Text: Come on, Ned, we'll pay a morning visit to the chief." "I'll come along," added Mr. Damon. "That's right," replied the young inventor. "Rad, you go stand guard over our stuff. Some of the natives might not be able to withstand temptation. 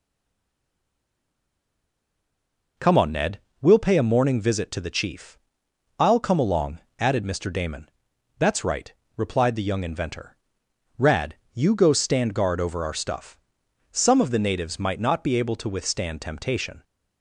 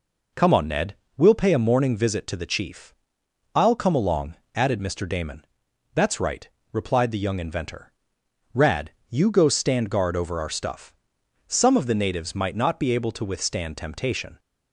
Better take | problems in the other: second | stays silent before the first word; strong; until 2.7 s; 2.7 s long

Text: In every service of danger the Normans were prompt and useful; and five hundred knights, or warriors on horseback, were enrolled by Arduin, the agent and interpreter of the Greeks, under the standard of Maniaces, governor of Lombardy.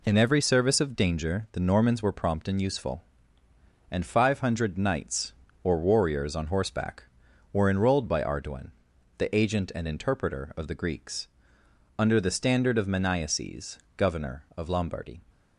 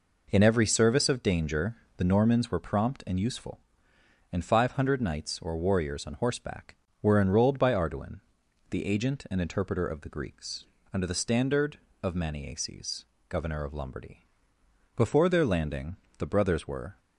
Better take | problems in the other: first | pauses between "danger" and "the"; slight; at 1.7 s; 0.20 s long // goes on to say "Before their landing the brothers were"; strong; from 14.9 s on; 2.0 s long

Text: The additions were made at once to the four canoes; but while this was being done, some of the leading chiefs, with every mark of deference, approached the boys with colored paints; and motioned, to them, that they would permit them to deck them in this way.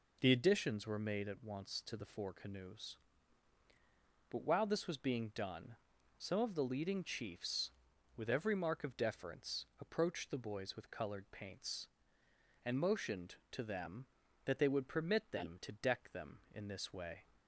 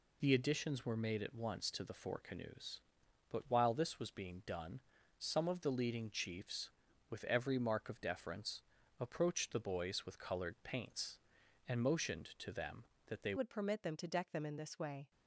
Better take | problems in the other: first | changes voice at "would"; from 13.3 s on; 1.8 s long

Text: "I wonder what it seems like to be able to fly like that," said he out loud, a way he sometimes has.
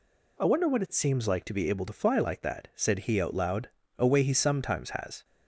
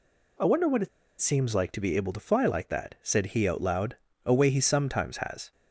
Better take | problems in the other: first | pauses between "it" and "seems"; slight; at 0.8 s; 0.32 s long

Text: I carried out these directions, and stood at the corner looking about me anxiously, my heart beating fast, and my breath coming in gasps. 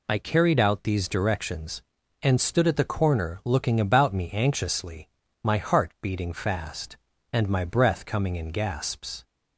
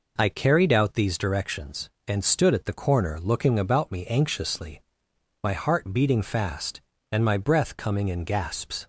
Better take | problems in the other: neither | none

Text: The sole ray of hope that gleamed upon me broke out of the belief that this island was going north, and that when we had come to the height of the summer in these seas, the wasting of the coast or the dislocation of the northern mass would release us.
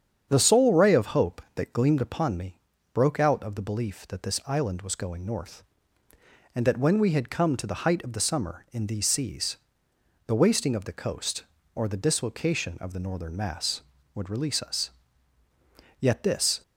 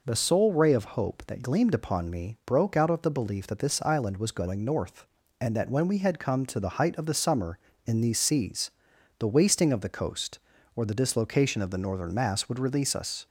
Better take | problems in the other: second | starts louder than the rest; strong; until 1.2 s; 8 dB // pauses between "me" and "broke"; at 2.5 s; 0.40 s long // goes on to say "Yet this"; noticeable; from 15.9 s on; 0.62 s long

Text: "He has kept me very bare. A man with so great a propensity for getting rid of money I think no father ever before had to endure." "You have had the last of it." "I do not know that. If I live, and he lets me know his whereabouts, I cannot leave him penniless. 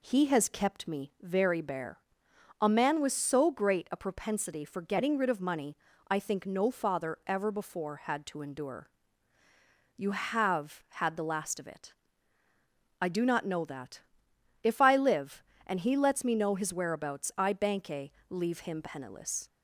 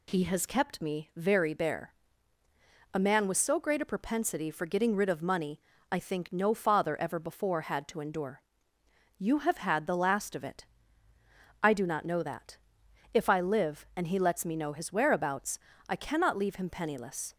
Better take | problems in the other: second | pauses between "money" and "I"; slight; at 5.7 s; 0.34 s long; slight in the second // says "banke" for "cannot"; at 17.5 s

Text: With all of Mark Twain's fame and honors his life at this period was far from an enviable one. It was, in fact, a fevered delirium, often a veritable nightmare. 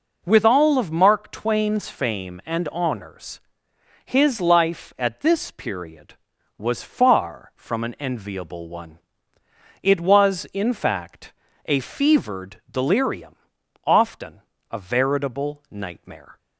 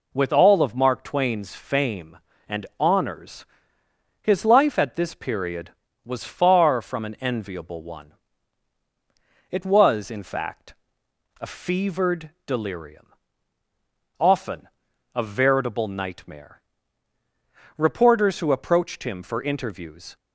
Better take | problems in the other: first | pauses between "honors" and "his"; noticeable; at 3.4 s; 0.76 s long; noticeable in the first // pauses between "fevered" and "delirium"; slight; at 12.2 s; 0.16 s long // pauses between "often" and "a"; noticeable; at 14.6 s; 0.46 s long; slight in the first // goes on to say "Reporters who approached him for interviews"; strong; from 17.7 s on; 2.3 s long

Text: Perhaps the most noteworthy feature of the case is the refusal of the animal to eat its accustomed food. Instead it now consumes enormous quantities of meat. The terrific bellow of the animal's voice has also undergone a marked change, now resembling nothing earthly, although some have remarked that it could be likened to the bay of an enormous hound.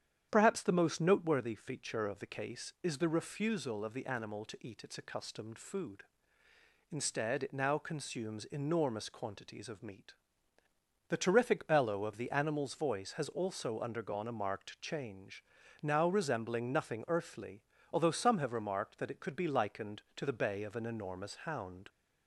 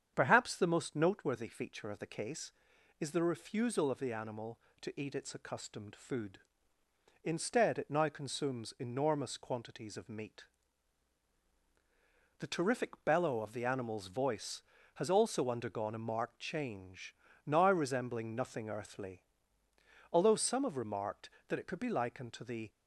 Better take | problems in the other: first | starts louder than the rest; strong; until 1.1 s; 8 dB; strong in the first // stops before "bay of an enormous hound"; at 22.6 s

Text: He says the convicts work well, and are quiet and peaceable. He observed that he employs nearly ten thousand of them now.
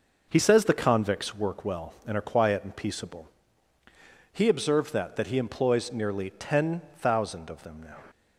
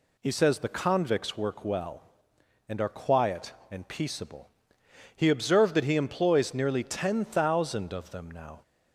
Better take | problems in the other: second | says "that" twice; at 5.1 s // pauses between "ten" and "thousand"; slight; at 6.8 s; 0.18 s long

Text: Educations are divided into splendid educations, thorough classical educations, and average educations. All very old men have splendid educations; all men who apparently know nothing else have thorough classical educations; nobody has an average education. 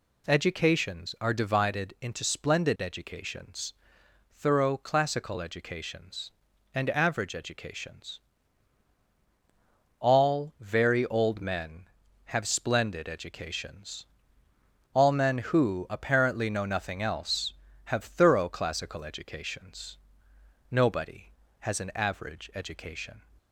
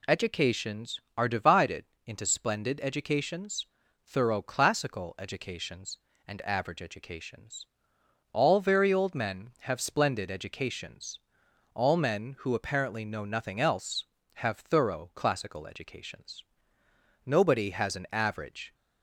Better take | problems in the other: first | pauses between "divided" and "into"; slight; at 1.8 s; 0.18 s long // stops before "education"; at 18.7 s

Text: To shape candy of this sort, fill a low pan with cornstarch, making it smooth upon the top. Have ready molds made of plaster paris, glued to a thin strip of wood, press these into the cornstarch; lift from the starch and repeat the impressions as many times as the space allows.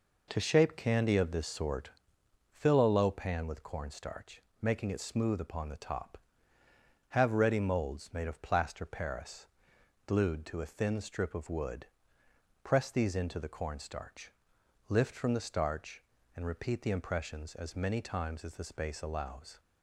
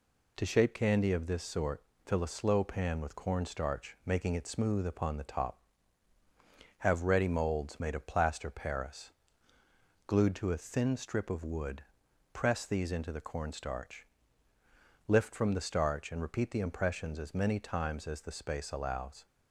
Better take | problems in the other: first | says "slow" for "low"; at 2.2 s

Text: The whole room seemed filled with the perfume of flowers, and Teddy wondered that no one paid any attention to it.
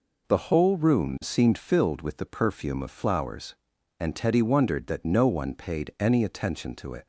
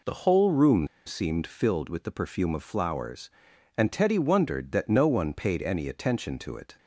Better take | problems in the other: first | pauses between "room" and "seemed"; slight; at 0.8 s; 0.20 s long

